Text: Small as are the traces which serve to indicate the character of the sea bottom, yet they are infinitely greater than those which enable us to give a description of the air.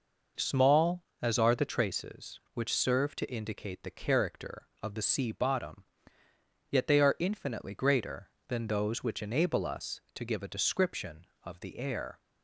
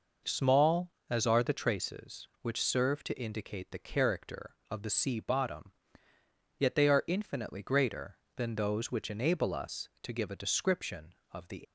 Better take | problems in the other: first | stops before "air"; at 11.6 s

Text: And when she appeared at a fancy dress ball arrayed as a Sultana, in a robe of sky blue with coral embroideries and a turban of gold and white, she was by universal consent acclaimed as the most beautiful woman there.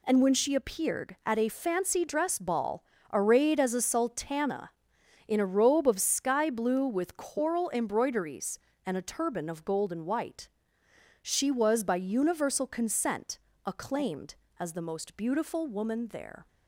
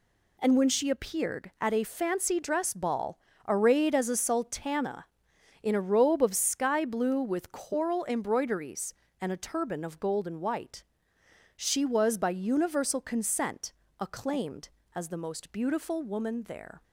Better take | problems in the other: neither | pauses between "ball" and "arrayed"; slight; the same in both // pauses between "consent" and "acclaimed"; slight; the same in both

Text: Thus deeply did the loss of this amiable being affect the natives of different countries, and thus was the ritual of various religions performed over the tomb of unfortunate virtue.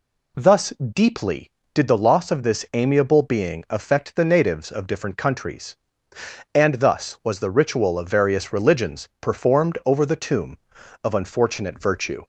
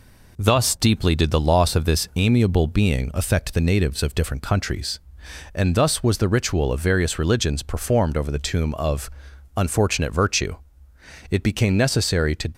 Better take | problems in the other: first | pauses between "of" and "unfortunate"; noticeable; at 9.0 s; 0.46 s long // goes on to say "It became necessary to"; noticeable; from 11.3 s on; 1.2 s long

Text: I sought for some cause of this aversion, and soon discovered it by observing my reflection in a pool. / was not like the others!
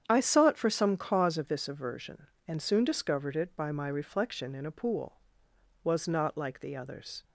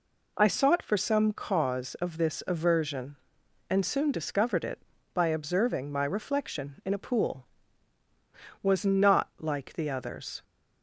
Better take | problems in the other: second | starts louder than the rest; strong; until 1.0 s; 8.5 dB // skips "observing"; at 3.7 s

